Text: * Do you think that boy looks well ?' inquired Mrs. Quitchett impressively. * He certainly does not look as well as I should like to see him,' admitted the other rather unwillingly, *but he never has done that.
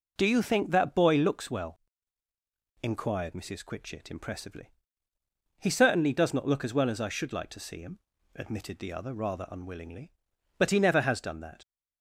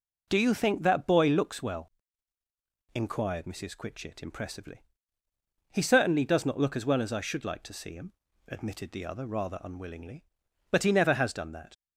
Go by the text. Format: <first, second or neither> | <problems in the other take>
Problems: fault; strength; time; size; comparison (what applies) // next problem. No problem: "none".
neither | starts louder than the rest; noticeable; the same in both